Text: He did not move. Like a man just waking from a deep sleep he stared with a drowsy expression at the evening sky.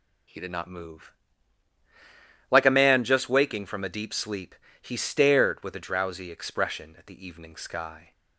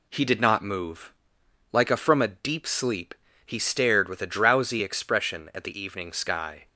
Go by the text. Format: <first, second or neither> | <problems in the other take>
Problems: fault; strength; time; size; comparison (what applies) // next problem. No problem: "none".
first | skips "man just waking"; at 1.9 s // pauses between "sleep" and "he"; slight; at 3.1 s; 0.32 s long; slight in the first